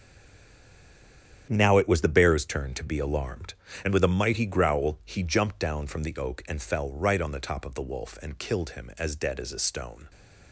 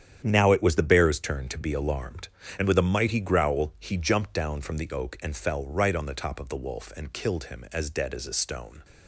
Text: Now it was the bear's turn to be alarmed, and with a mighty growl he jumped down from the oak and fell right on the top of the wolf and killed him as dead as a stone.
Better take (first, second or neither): second